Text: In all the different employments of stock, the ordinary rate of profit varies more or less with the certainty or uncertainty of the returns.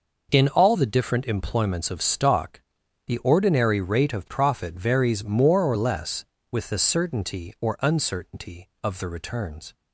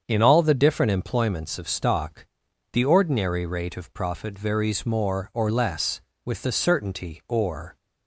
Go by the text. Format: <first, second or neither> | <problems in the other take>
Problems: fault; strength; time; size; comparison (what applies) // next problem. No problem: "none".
first | starts louder than the rest; strong; until 1.0 s; 7.5 dB // stops before "uncertainty of the returns"; at 7.7 s